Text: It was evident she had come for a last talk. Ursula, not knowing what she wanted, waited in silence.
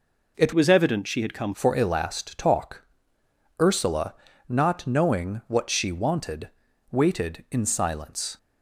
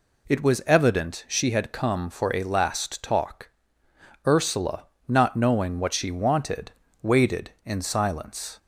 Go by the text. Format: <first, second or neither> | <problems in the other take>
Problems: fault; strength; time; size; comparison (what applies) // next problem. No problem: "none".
second | changes voice from "was" to "come"; from 0.5 to 1.5 s; 1.0 s long